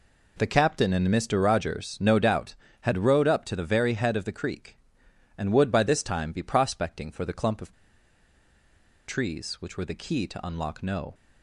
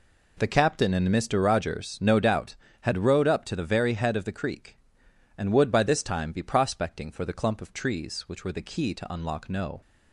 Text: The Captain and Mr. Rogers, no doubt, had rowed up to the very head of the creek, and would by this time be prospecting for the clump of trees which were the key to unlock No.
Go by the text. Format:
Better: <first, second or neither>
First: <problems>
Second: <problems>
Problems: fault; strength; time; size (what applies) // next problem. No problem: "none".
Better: second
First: pauses between "of" and "trees"; strong; at 7.7 s; 1.3 s long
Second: none